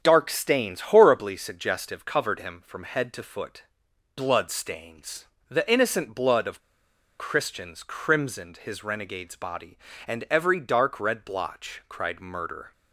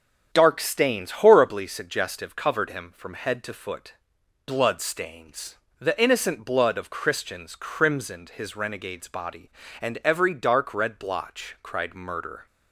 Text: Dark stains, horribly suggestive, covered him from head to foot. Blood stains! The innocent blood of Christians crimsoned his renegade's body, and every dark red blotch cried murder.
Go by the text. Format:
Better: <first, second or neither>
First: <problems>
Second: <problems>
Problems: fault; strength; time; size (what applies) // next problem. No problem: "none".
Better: second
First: starts louder than the rest; strong; until 1.0 s; 8 dB // pauses between "of" and "Christians"; noticeable; at 6.5 s; 0.60 s long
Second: starts louder than the rest; strong; until 1.3 s; 8 dB